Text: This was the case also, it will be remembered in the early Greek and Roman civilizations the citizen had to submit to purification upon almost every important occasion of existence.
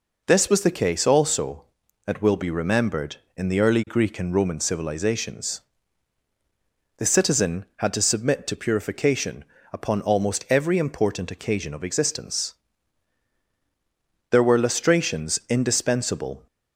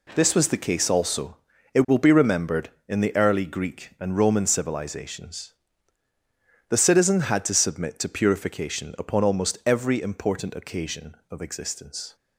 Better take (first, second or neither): second